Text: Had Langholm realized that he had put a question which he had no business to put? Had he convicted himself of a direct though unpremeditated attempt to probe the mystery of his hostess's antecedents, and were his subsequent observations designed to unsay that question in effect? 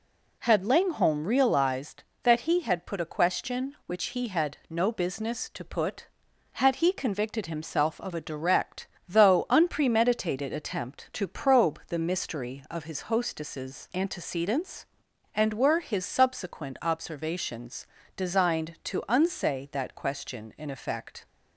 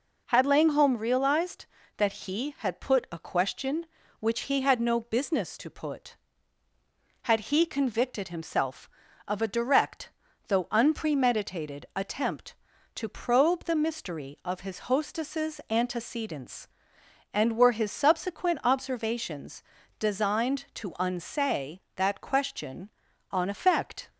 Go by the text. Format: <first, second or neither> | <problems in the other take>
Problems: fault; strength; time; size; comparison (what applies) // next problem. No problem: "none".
first | pauses between "direct" and "though"; at 10.1 s; 0.38 s long; slight in the first // pauses between "observations" and "designed"; slight; at 19.6 s; 0.36 s long; slight in the first // says "on" for "in"; at 23.3 s